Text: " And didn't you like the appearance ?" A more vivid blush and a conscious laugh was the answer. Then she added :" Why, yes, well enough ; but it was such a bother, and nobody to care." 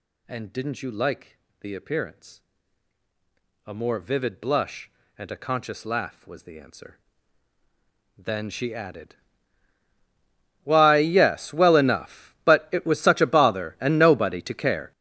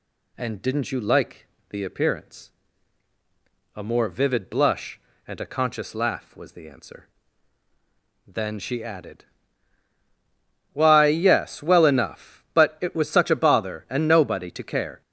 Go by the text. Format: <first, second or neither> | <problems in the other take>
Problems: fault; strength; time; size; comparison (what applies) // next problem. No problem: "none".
second | gets louder; strong; throughout; 15 dB // pauses between "like" and "the"; slight; at 1.3 s; 0.22 s long; slight in the second